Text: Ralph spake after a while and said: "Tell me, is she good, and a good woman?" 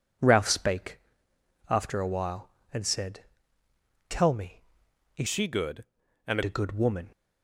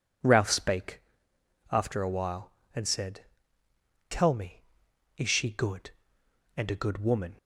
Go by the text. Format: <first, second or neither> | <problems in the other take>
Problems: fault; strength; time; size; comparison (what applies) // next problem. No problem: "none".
second | pauses between "spake" and "after"; noticeable; at 0.9 s; 0.70 s long; noticeable in the second // changes voice from "she" to "and"; from 5.2 to 6.4 s; 1.2 s long